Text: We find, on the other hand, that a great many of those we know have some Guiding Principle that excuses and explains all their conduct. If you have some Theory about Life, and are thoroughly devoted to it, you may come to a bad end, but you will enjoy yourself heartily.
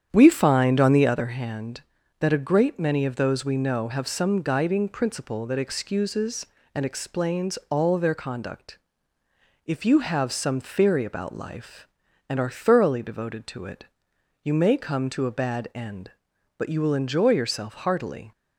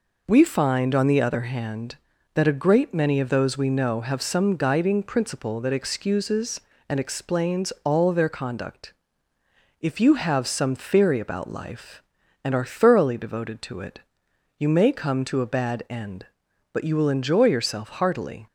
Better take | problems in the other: second | starts louder than the rest; strong; until 1.3 s; 9 dB

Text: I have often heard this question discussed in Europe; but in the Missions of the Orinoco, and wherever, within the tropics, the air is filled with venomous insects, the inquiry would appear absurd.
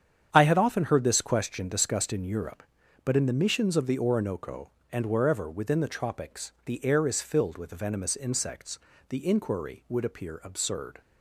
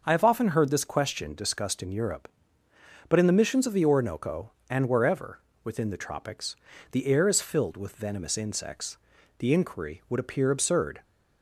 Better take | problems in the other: second | starts louder than the rest; strong; until 1.3 s; 8.5 dB; also in the second // says "had" for "have"; at 0.4 s

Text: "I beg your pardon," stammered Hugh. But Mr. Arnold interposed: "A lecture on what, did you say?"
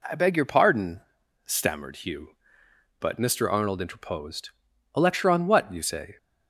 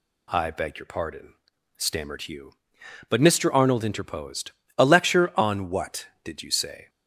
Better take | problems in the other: second | skips "did"; at 5.7 s

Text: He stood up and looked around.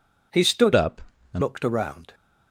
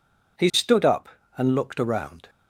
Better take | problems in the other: second | changes voice from "up" to "and"; from 0.7 to 1.4 s; 0.7 s long

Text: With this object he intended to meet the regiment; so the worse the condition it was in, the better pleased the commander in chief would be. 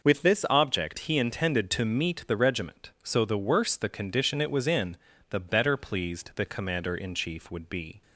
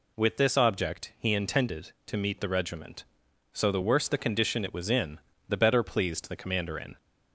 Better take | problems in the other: first | stops before "chief would be"; at 6.9 s

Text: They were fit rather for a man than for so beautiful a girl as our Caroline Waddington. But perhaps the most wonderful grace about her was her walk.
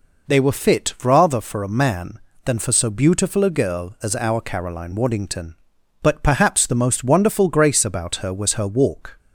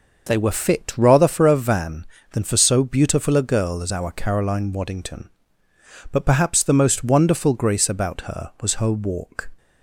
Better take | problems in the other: first | says "van" for "man"; at 1.5 s

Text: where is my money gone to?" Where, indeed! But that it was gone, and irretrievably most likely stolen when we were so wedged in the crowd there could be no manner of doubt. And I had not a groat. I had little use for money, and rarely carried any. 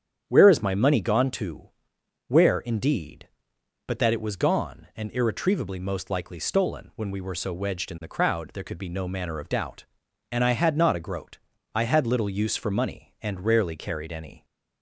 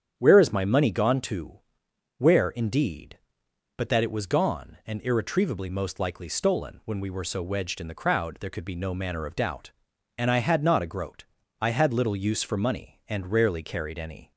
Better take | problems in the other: neither | starts louder than the rest; strong; the same in both

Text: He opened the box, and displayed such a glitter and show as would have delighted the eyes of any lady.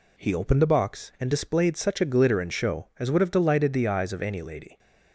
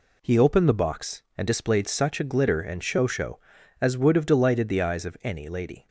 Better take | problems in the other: first | says "show" twice; at 3.0 s

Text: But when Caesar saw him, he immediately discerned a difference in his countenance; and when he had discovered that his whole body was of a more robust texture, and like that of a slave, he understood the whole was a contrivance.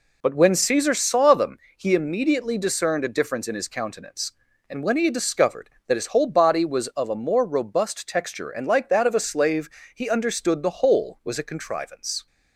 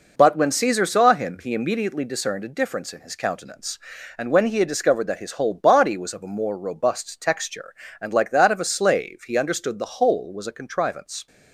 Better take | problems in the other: second | says "them" for "him"; at 1.3 s

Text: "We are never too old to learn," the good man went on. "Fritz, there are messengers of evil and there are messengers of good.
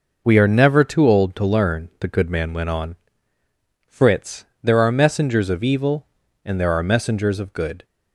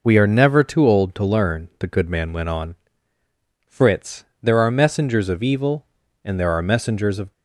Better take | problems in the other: first | stops before "good"; at 7.3 s

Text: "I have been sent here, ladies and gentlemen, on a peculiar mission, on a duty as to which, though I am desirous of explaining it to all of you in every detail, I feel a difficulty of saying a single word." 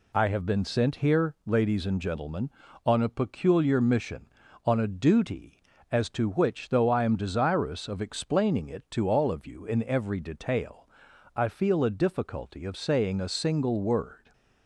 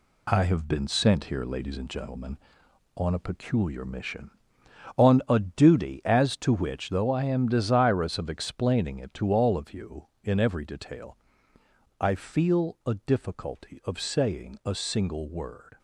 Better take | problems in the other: first | gets quieter; throughout; 6.5 dB

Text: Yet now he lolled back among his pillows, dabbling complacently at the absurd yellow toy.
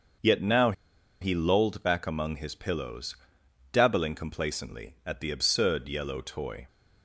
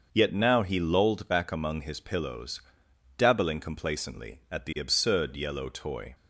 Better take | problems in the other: second | starts louder than the rest; until 1.7 s; 6.5 dB; also in the second // pauses between "now" and "he"; noticeable; at 0.7 s; 0.48 s long

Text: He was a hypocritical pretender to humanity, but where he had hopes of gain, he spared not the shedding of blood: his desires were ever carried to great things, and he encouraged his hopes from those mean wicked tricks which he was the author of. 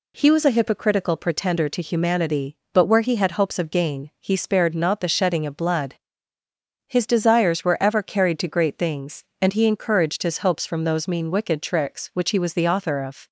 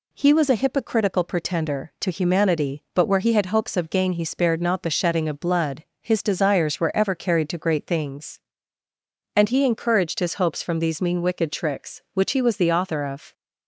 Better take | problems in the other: first | says "these" for "those"; at 10.7 s

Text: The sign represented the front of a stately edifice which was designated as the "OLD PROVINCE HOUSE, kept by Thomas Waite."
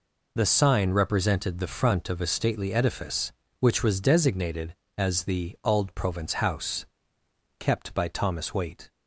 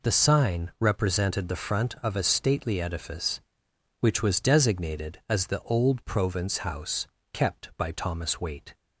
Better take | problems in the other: neither | none

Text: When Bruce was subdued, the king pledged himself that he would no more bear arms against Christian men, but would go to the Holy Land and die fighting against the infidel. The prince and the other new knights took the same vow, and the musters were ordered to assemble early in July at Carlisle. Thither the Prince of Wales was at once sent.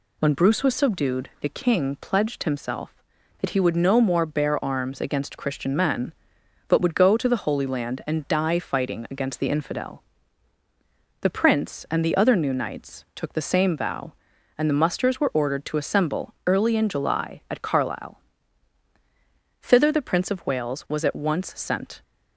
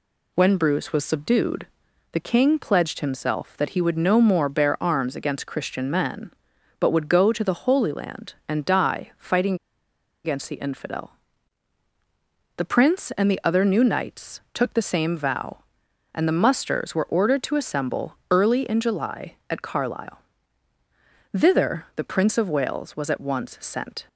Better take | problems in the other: first | pauses between "fighting" and "against"; noticeable; at 9.5 s; 0.70 s long // pauses between "assemble" and "early"; slight; at 18.1 s; 0.16 s long

